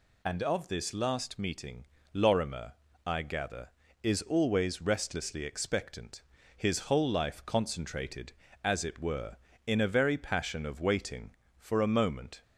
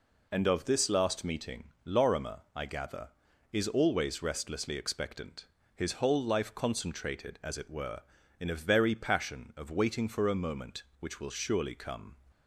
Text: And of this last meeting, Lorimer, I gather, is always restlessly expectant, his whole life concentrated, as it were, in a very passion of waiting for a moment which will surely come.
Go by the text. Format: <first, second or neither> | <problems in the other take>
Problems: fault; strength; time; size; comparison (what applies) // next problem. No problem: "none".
second | stops before "which will surely come"; at 12.4 s